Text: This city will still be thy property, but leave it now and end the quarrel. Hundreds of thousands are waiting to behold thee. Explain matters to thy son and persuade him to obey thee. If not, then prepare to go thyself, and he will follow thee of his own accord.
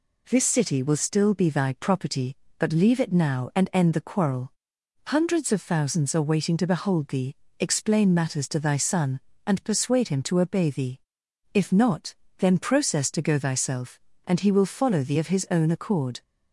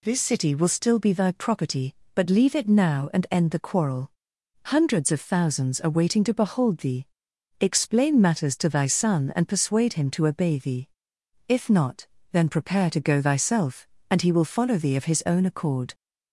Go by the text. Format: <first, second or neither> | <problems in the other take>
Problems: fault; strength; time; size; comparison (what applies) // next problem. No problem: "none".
second | says "process" for "prepare"; at 12.5 s